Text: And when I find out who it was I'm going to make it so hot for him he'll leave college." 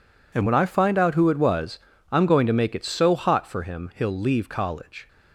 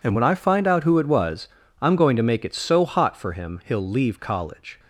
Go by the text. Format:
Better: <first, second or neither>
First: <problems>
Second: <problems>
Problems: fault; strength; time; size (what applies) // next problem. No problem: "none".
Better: neither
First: pauses between "was" and "I'm"; slight; at 1.7 s; 0.35 s long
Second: pauses between "was" and "I'm"; slight; at 1.4 s; 0.36 s long